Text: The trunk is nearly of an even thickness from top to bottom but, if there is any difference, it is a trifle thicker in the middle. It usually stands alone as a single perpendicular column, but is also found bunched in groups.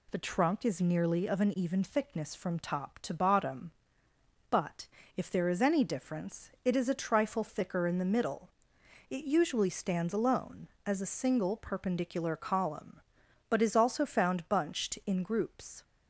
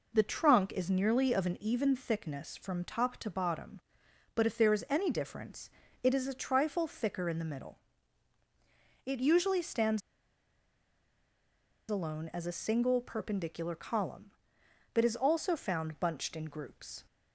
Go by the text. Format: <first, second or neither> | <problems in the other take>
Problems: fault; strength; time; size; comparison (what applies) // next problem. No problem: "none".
first | pauses between "stands" and "alone"; strong; at 10.0 s; 1.8 s long